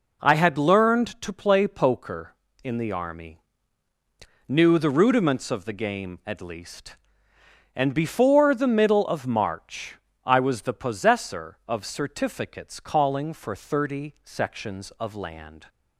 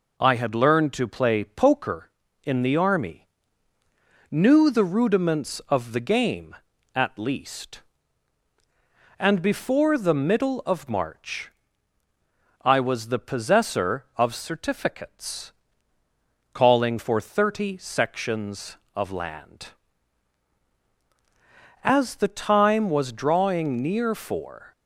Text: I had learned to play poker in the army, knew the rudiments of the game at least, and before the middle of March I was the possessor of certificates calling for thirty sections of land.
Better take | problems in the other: first | pauses between "March" and "I"; at 11.5 s; 1.1 s long; slight in the first // pauses between "certificates" and "calling"; at 15.5 s; 1.0 s long // goes on to say "As the time was drawing near for"; strong; from 21.8 s on; 2.8 s long

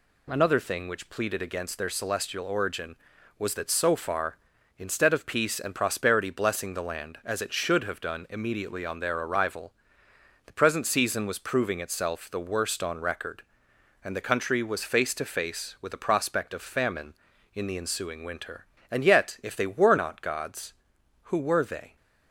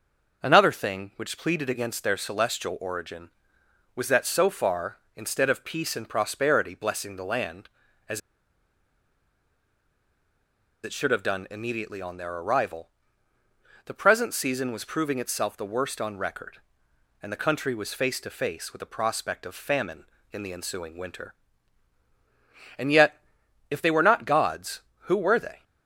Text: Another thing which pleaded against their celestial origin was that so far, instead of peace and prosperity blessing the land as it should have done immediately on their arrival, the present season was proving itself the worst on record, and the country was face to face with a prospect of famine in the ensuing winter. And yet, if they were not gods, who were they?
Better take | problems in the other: first | pauses between "as" and "it"; strong; at 8.1 s; 2.6 s long

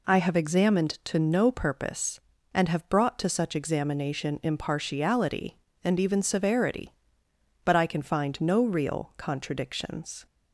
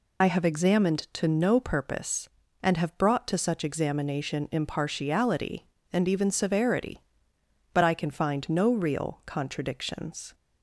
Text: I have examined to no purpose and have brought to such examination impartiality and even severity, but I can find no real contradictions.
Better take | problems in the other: first | loses the start of "I"; at 0.2 s; 50 ms

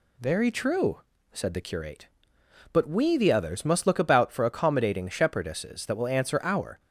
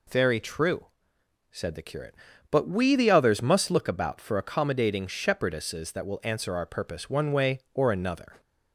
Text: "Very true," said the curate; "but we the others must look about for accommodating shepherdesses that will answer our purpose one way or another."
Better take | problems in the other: second | stops before "purpose one way or another"; at 6.7 s

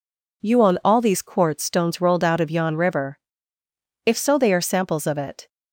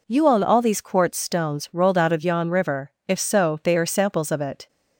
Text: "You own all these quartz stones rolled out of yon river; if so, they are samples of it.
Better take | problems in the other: neither | none

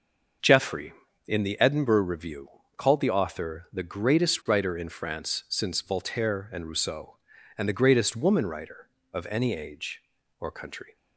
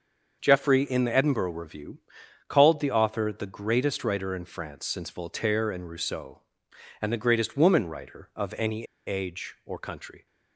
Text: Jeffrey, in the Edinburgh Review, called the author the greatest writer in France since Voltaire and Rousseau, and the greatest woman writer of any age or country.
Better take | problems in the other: first | starts louder than the rest; until 1.4 s; 6 dB; also in the first // pauses between "any" and "age"; slight; at 8.8 s; 0.21 s long

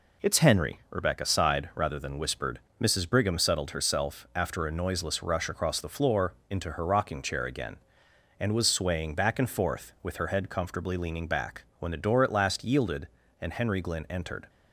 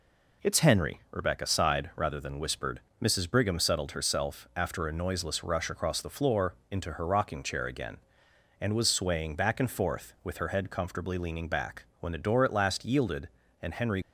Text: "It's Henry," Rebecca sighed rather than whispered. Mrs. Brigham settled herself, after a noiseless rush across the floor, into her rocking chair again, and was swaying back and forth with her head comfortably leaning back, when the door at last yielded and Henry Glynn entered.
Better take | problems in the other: first | stops before "Glynn entered"; at 14.0 s

